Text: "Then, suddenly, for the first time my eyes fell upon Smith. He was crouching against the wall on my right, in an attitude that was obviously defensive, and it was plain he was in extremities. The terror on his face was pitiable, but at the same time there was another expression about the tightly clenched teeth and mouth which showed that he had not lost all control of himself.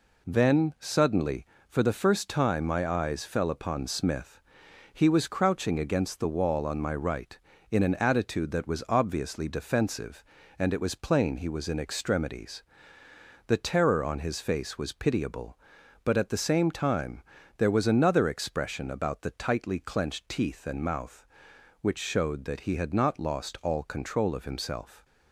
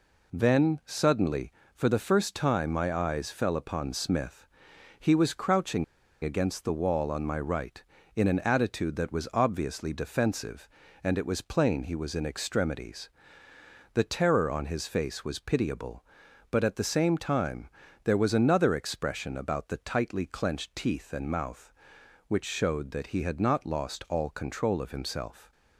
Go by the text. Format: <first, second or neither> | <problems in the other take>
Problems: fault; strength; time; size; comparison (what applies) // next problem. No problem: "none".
first | pauses between "crouching" and "against"; at 5.8 s; 0.38 s long // pauses between "time" and "there"; slight; at 17.6 s; 0.34 s long; slight in the first